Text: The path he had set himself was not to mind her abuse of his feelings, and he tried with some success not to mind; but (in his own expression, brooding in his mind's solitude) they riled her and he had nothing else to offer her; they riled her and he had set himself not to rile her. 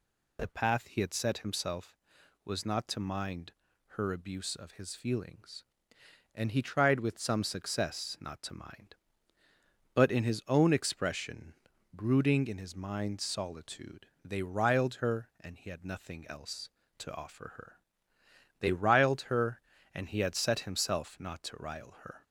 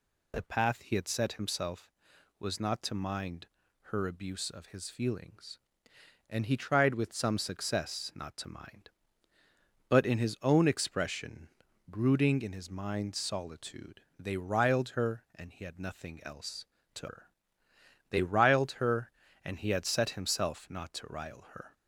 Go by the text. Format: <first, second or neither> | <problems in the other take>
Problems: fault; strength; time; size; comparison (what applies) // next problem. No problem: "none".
first | pauses between "mind" and "her"; slight; at 3.4 s; 0.36 s long; slight in the first // skips "offer"; at 17.0 s